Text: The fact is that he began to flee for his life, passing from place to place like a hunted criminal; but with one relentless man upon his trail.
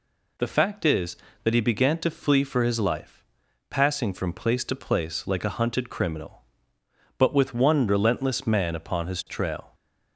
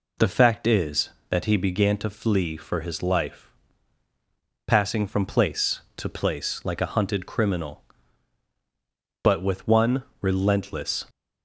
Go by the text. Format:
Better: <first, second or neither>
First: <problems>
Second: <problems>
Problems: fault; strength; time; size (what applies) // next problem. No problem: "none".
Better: first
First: none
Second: pauses between "one" and "relentless"; slight; at 10.0 s; 0.16 s long // stops before "man upon his trail"; at 11.0 s